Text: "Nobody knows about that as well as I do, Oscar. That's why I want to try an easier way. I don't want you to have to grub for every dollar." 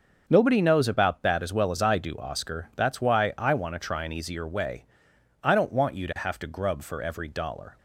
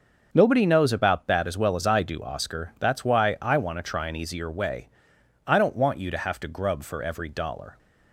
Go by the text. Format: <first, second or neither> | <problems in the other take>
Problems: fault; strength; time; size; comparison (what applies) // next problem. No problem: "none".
neither | starts louder than the rest; the same in both